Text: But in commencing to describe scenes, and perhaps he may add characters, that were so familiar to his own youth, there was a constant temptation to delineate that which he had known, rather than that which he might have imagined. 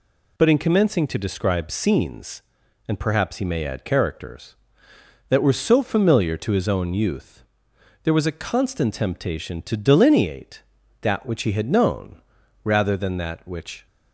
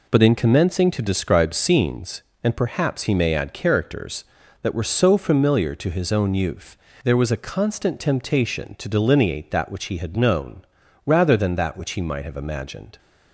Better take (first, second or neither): second